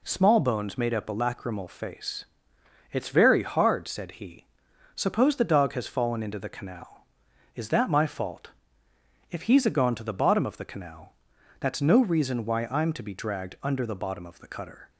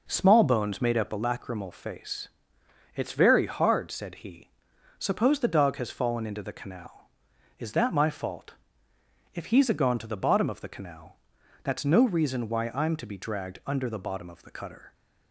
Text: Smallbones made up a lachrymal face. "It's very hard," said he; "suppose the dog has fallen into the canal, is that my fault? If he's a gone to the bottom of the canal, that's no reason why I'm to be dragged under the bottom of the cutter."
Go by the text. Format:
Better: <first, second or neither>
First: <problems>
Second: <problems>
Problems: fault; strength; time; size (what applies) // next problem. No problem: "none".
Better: first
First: none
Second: starts louder than the rest; noticeable; until 1.2 s; 5 dB